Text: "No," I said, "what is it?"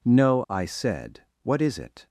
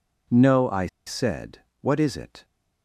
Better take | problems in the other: first | pauses between "I" and "said"; slight; at 0.8 s; 0.19 s long

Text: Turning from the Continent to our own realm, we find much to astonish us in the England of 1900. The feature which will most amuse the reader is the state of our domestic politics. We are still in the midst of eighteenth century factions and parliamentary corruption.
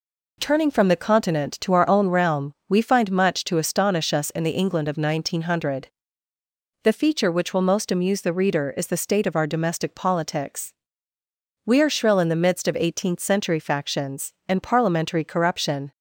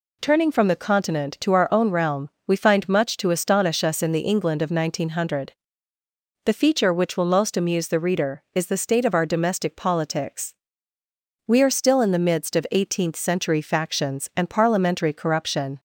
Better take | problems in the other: second | says "shrill" for "still"; at 11.8 s

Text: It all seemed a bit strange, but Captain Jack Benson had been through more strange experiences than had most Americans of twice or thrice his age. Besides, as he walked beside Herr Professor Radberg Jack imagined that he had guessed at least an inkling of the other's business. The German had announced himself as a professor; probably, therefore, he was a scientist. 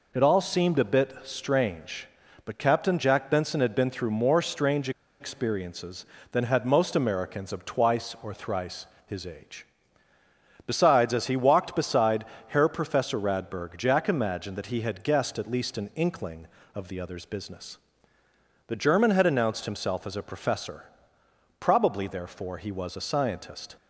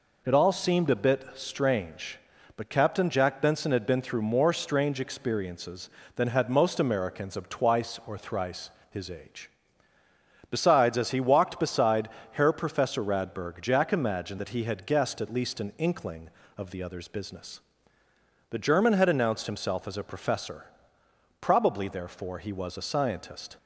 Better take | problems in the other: second | pauses between "strange" and "experiences"; slight; at 4.8 s; 0.30 s long // pauses between "thrice" and "his"; slight; at 8.8 s; 0.20 s long; slight in the second // pauses between "beside" and "Herr"; slight; at 12.2 s; 0.26 s long; slight in the second

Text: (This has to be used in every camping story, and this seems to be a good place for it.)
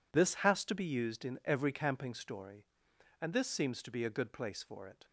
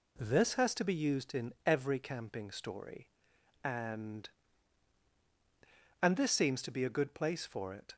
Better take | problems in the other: first | says "and" twice; at 6.0 s

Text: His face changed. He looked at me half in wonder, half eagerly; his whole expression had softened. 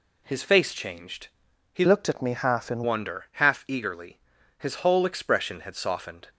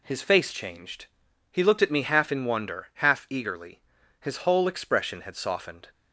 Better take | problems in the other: second | changes voice from "looked" to "in"; from 1.8 to 2.8 s; 1.0 s long

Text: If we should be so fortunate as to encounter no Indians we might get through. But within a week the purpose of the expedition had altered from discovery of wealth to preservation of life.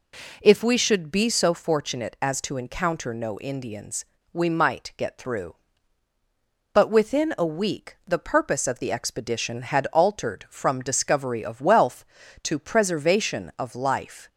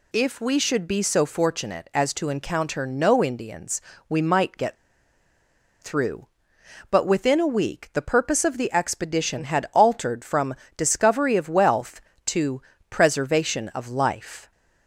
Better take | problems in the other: first | pauses between "Indians" and "we"; slight; at 3.7 s; 0.30 s long; slight in the first // pauses between "get" and "through"; at 4.7 s; 1.0 s long // pauses between "from" and "discovery"; slight; at 10.5 s; 0.24 s long // pauses between "to" and "preservation"; slight; at 12.6 s; 0.30 s long

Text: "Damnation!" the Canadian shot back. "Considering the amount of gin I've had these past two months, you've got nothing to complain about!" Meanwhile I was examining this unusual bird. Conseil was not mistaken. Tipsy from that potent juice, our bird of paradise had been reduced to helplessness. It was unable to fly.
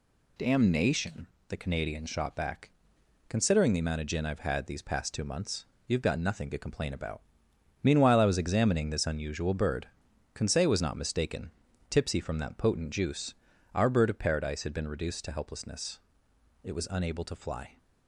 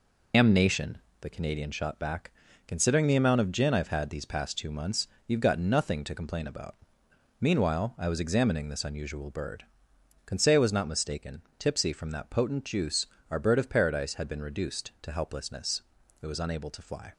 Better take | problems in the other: first | loses the start of "Damnation"; at 0.3 s; 105 ms

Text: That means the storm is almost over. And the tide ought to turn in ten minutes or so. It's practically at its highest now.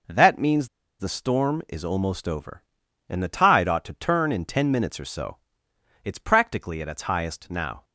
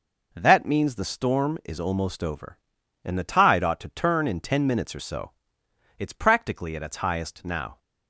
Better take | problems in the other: second | pauses between "means" and "the"; slight; at 0.6 s; 0.32 s long

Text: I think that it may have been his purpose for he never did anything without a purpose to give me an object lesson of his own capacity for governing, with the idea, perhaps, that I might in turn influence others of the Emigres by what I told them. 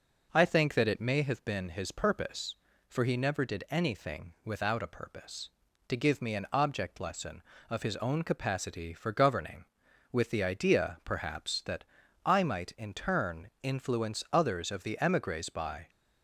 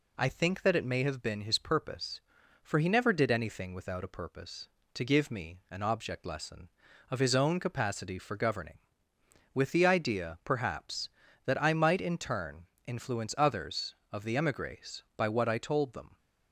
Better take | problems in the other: second | pauses between "that" and "I"; at 11.8 s; 0.40 s long // pauses between "turn" and "influence"; slight; at 13.4 s; 0.16 s long; slight in the second // stops before "what I told them"; at 15.8 s

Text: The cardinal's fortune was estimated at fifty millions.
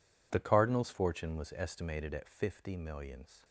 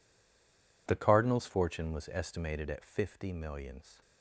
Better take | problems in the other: first | stays silent before the first word; slight; until 0.8 s; 0.8 s long

